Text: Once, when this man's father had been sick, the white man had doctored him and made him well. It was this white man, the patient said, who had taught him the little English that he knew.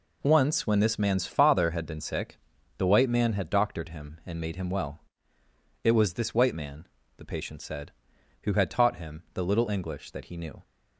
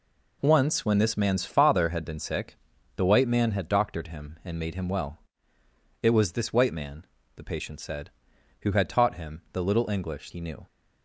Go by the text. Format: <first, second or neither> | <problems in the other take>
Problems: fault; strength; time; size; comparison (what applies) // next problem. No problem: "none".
first | skips "that"; at 10.3 s